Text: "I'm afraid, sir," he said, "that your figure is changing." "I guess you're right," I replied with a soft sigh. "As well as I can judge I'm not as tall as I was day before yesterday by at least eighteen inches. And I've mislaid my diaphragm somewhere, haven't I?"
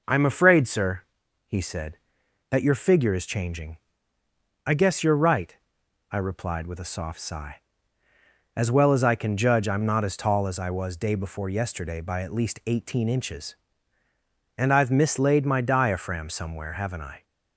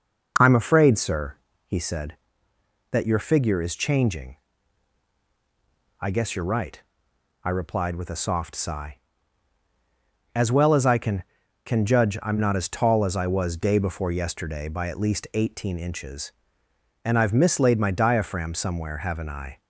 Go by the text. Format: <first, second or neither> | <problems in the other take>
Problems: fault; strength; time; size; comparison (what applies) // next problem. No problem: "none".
first | says "can" twice; at 11.6 s